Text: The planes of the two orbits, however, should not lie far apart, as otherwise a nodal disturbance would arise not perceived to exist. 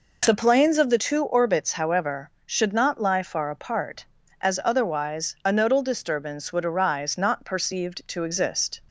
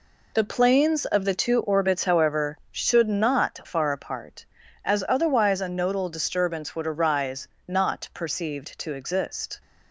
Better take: first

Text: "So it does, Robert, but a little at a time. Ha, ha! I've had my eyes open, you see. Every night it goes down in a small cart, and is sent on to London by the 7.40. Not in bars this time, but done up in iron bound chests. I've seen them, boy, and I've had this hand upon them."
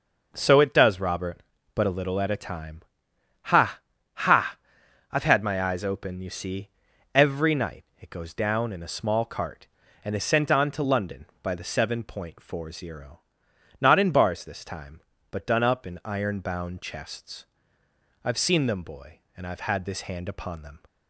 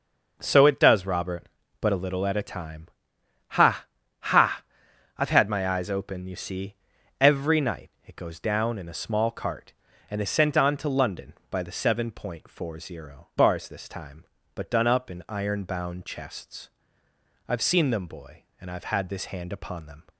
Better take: first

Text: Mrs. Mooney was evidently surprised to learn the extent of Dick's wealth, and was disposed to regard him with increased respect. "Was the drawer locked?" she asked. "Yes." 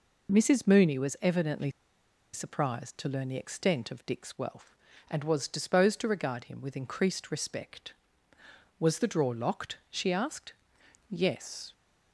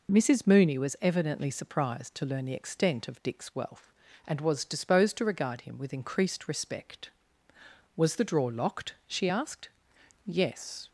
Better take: second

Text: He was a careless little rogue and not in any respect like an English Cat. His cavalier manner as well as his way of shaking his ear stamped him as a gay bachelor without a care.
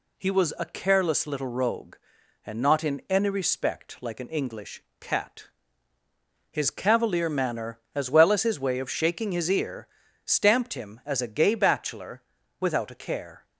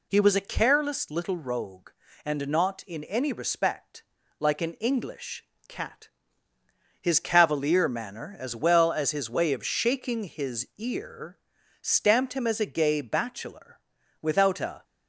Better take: first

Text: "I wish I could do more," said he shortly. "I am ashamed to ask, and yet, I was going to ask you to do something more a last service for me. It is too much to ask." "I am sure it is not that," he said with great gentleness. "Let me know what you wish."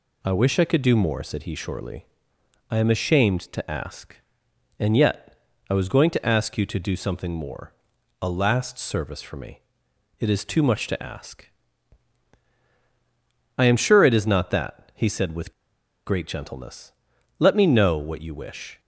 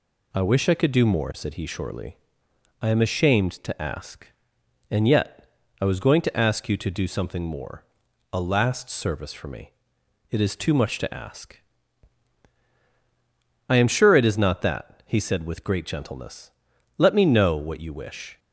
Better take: second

